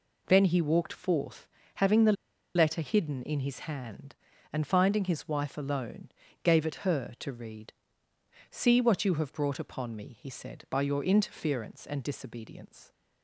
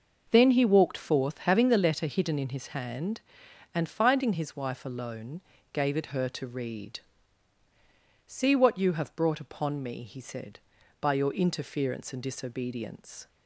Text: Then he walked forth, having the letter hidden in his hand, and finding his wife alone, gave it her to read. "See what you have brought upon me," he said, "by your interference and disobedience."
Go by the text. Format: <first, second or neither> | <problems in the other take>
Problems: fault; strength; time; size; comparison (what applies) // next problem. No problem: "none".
second | pauses between "the" and "letter"; at 2.1 s; 0.42 s long